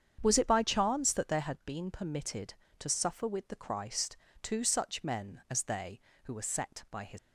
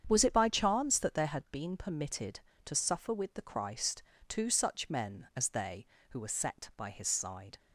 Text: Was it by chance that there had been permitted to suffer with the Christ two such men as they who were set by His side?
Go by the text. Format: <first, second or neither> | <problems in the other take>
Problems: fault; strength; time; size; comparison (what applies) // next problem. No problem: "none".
second | starts louder than the rest; strong; until 1.2 s; 8 dB; strong in the second // pauses between "Christ" and "two"; slight; at 4.1 s; 0.24 s long; slight in the second // stops before "side"; at 7.1 s